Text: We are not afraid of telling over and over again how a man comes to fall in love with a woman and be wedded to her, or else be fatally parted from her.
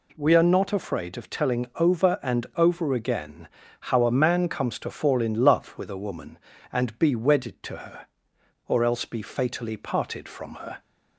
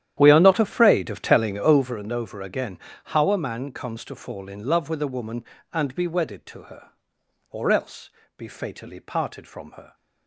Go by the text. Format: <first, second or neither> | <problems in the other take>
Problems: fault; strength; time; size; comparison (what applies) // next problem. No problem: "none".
first | starts louder than the rest; strong; until 2.0 s; 11 dB // pauses between "again" and "how"; slight; at 2.7 s; 0.28 s long; slight in the first // pauses between "else" and "be"; slight; at 8.1 s; 0.26 s long